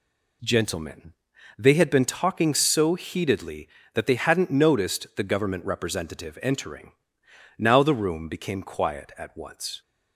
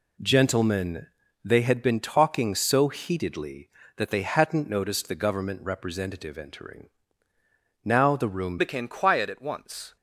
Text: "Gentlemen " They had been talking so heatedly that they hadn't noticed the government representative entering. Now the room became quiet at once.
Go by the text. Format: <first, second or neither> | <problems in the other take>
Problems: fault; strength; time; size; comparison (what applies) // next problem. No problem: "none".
first | changes voice at "became"; from 8.5 s on; 1.4 s long